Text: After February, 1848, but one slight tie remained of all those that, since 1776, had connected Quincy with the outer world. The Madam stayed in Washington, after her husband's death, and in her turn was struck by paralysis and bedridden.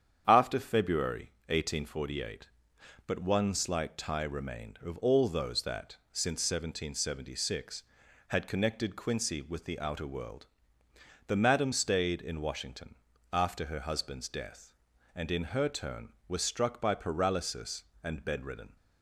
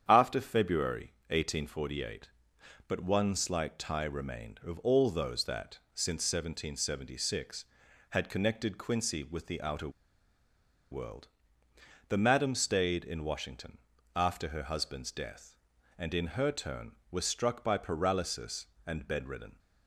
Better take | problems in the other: first | starts louder than the rest; strong; until 1.0 s; 8.5 dB; strong in the first // pauses between "outer" and "world"; at 9.8 s; 1.0 s long

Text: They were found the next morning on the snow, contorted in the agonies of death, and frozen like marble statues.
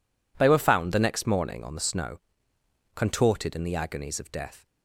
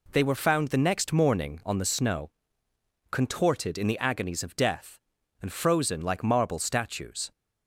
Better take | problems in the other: second | stops before "and frozen like marble statues"; at 4.6 s

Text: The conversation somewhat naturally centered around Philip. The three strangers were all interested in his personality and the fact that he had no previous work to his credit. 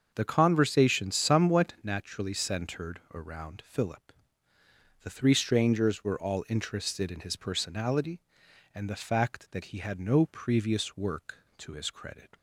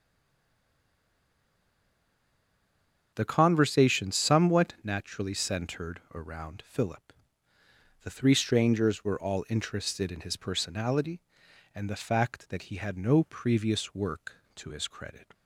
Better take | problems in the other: first | stays silent before the first word; strong; until 3.1 s; 3.1 s long // starts louder than the rest; until 4.1 s; 6.5 dB; also in the first

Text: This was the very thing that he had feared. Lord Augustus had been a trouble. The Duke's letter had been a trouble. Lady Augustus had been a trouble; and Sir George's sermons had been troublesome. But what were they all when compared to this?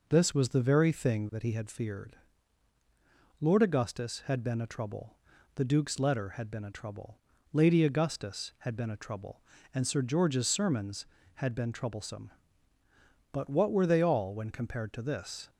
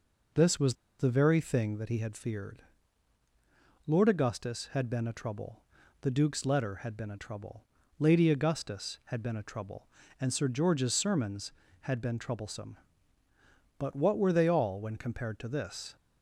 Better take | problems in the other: first | pauses between "was" and "the"; slight; at 0.7 s; 0.24 s long

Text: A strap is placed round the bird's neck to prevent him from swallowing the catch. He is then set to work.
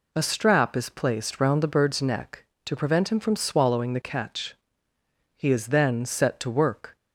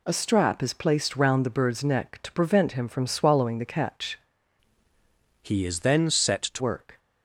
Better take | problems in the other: first | changes voice from "He" to "to"; from 5.4 to 6.6 s; 1.2 s long

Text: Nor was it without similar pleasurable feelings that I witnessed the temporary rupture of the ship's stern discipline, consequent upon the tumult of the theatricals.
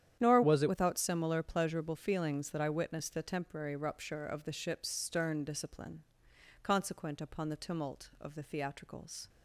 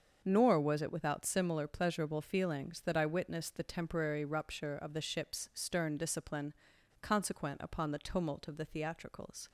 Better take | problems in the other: second | starts louder than the rest; strong; until 1.2 s; 10 dB; also in the second // changes voice from "was" to "it"; from 0.4 to 0.6 s; 0.2 s long

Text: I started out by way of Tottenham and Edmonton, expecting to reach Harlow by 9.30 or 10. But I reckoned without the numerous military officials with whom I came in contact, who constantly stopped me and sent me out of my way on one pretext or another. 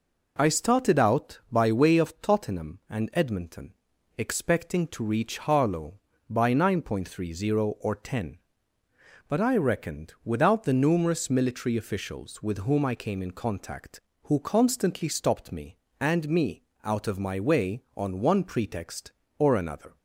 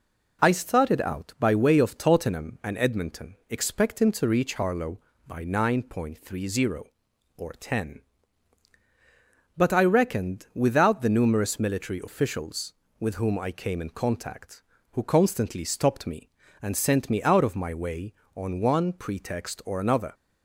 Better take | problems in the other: second | skips "sent"; at 16.2 s // pauses between "me" and "out"; slight; at 16.6 s; 0.24 s long

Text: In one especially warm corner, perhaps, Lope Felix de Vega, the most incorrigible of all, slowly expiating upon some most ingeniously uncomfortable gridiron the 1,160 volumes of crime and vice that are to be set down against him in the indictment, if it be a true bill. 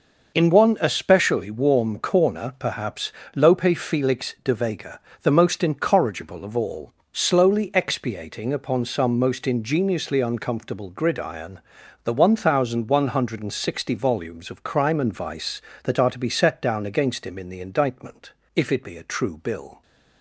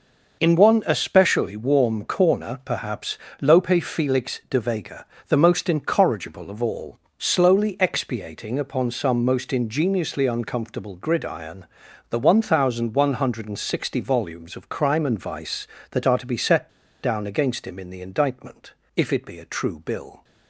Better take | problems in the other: first | pauses between "gridiron" and "the"; noticeable; at 11.6 s; 0.46 s long; noticeable in the first // pauses between "set" and "down"; slight; at 16.6 s; 0.34 s long

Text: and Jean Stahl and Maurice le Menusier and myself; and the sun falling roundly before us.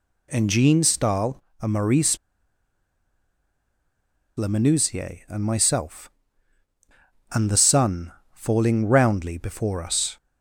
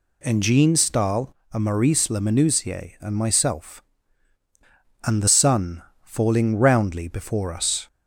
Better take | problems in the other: second | pauses between "Maurice" and "le"; strong; at 2.1 s; 2.2 s long // pauses between "sun" and "falling"; slight; at 8.1 s; 0.22 s long; slight in the second

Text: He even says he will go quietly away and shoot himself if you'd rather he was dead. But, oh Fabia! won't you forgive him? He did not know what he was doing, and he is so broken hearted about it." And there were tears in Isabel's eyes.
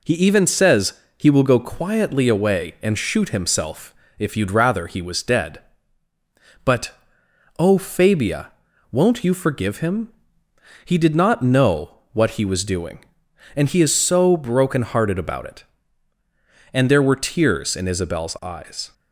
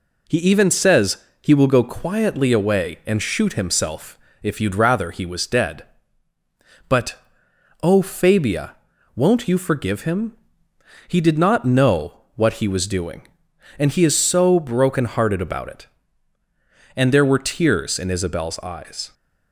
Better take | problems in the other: neither | pauses between "says" and "he"; slight; the same in both // pauses between "himself" and "if"; slight; the same in both

